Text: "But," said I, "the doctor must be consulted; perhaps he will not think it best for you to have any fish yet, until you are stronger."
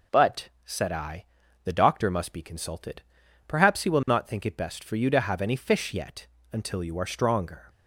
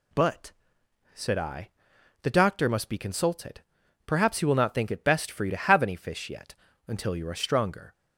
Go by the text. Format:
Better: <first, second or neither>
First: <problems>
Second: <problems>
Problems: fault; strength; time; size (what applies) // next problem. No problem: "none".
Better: neither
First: none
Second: none